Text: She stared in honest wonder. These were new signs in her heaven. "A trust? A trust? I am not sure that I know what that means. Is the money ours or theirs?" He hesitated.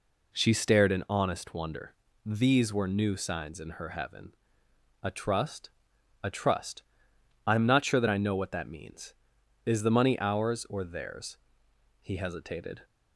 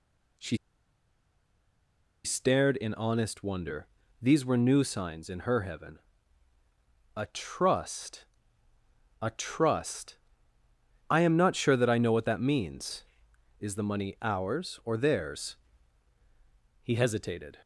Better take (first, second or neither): first